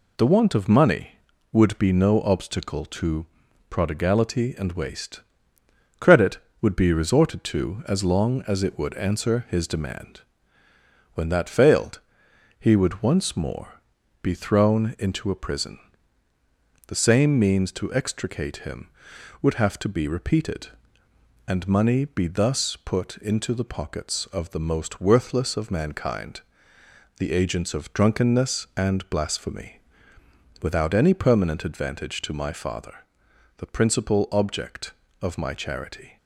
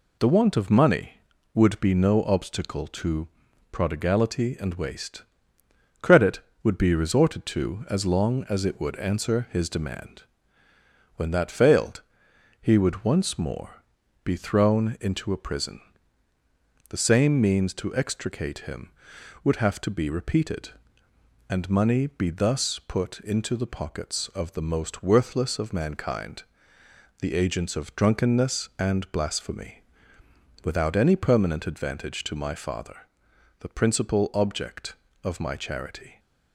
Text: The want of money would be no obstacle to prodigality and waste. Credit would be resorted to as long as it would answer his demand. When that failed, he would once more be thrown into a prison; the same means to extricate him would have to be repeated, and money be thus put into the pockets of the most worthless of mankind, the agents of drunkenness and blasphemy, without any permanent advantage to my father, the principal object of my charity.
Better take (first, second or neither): neither